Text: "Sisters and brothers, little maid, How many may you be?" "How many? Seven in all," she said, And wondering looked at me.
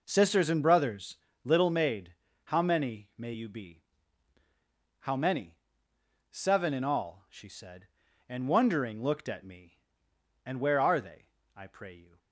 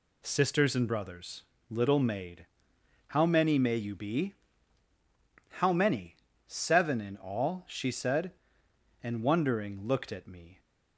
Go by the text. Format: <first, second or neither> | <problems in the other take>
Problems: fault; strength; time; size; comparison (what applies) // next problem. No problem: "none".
second | goes on to say "And where are they I pray you"; strong; from 10.4 s on; 1.7 s long